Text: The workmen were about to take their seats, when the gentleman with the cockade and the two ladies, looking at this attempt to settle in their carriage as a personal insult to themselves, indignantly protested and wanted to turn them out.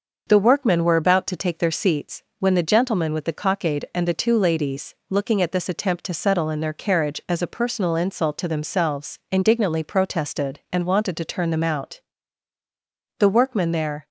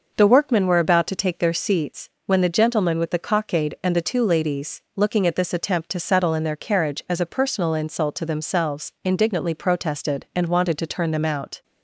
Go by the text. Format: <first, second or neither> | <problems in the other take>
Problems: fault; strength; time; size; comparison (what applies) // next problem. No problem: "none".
second | starts louder than the rest; noticeable; until 1.3 s; 6 dB // goes on to say "The workmen there"; noticeable; from 13.1 s on; 0.88 s long